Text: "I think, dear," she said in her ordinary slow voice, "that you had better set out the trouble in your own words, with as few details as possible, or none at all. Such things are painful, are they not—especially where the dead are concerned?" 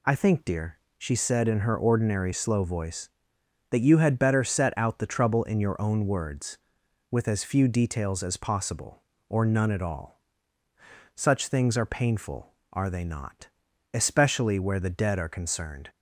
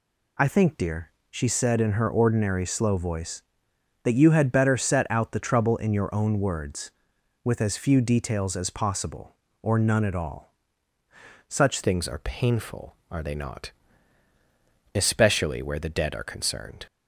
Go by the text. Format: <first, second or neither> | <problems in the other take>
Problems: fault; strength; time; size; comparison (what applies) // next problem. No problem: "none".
first | changes voice at "things"; from 11.8 s on; 5.0 s long